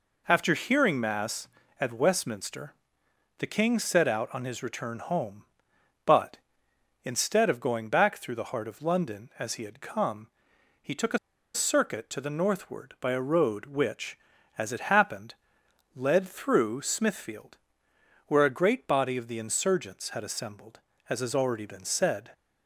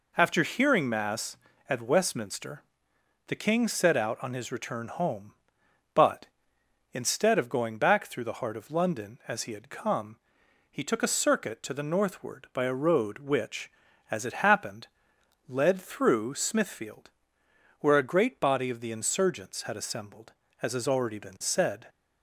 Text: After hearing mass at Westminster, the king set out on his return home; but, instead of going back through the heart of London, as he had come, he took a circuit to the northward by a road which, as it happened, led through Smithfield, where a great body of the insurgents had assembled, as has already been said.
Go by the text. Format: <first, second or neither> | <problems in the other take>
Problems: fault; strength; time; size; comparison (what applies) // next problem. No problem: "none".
second | pauses between "a" and "circuit"; at 11.1 s; 0.36 s long